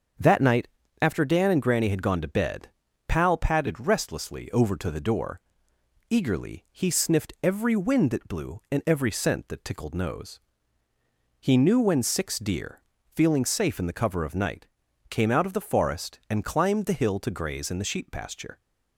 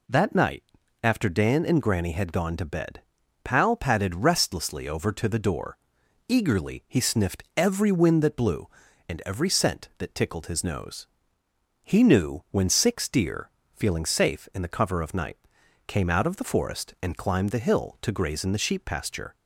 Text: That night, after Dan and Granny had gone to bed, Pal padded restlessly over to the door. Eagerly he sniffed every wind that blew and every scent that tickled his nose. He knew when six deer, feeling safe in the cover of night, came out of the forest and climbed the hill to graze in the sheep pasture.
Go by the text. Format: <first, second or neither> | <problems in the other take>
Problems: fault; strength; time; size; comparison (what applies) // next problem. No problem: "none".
second | starts louder than the rest; until 1.5 s; 7 dB // skips "his"; at 9.9 s